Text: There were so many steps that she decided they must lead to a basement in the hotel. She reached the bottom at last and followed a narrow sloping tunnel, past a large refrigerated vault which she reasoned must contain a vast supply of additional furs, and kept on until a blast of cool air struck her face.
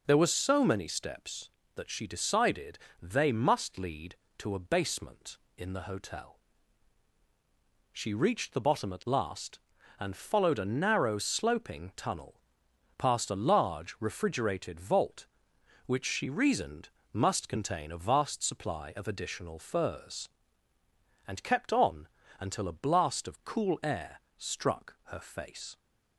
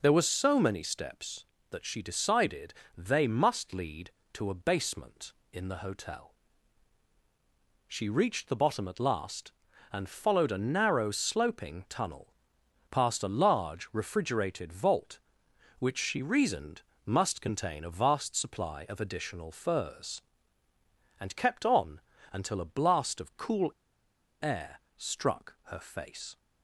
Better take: first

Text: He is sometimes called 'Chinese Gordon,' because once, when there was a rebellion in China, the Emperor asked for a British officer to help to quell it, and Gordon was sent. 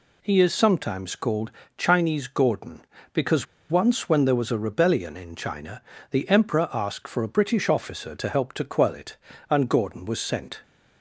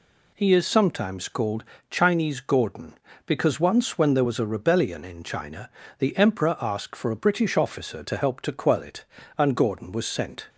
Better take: second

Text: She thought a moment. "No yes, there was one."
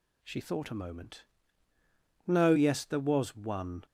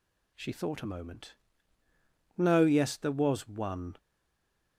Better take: first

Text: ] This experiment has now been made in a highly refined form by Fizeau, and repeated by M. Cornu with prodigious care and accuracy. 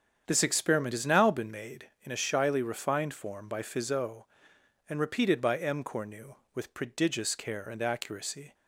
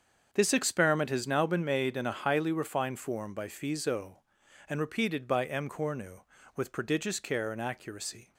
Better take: second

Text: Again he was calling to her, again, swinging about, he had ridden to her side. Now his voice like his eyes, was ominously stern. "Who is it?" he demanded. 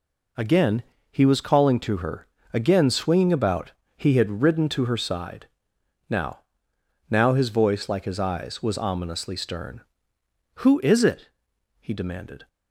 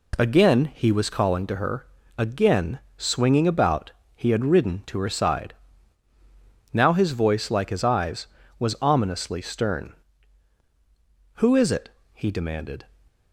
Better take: second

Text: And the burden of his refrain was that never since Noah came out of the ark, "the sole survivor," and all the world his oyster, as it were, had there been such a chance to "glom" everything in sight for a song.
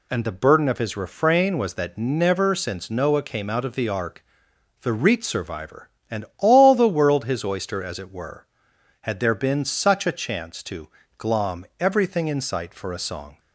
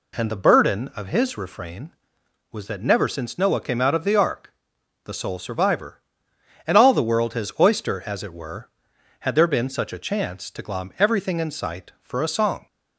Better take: second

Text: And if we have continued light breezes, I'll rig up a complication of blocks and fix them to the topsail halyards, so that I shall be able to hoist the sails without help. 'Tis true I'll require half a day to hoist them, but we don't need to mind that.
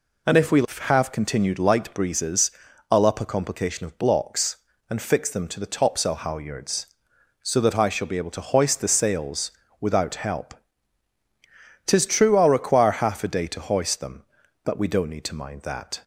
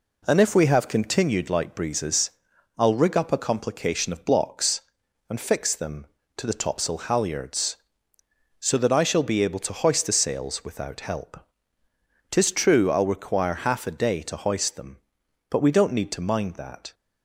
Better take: second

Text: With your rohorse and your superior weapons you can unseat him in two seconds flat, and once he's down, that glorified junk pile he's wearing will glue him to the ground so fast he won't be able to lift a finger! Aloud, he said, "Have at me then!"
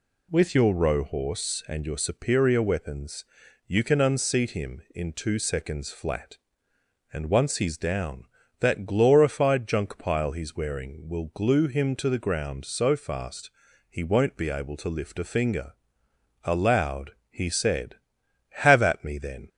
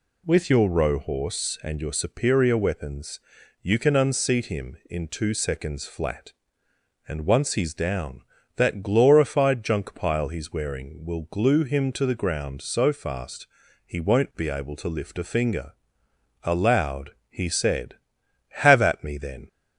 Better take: neither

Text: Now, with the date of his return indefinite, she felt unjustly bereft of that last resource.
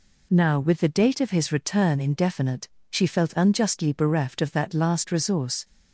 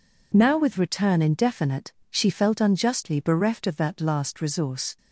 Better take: first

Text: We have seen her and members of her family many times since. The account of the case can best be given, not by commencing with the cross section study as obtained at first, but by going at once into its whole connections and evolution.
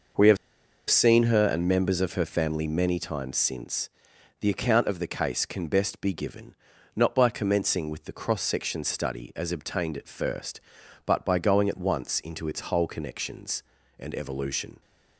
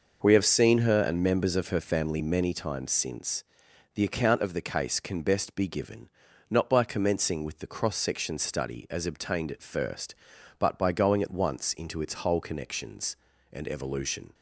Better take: second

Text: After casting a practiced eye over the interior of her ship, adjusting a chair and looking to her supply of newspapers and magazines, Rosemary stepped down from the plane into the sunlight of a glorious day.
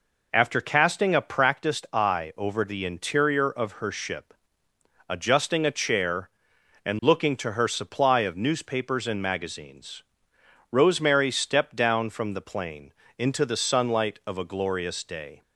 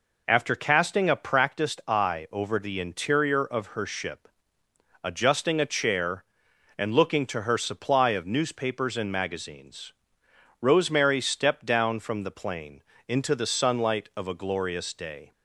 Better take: neither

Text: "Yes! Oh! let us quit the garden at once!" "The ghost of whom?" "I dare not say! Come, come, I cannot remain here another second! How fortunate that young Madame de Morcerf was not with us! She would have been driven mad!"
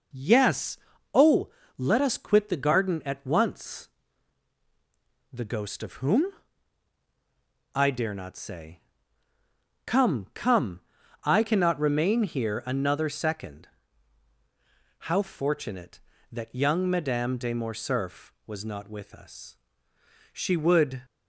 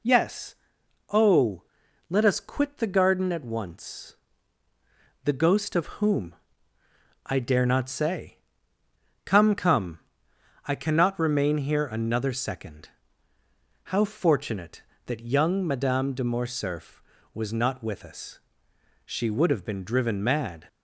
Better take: second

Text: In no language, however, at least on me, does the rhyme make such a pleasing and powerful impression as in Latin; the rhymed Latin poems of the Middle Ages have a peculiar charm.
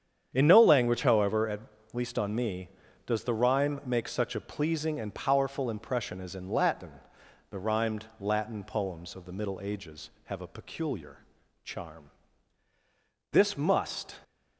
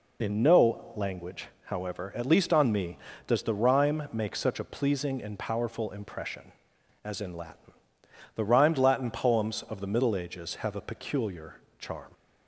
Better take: second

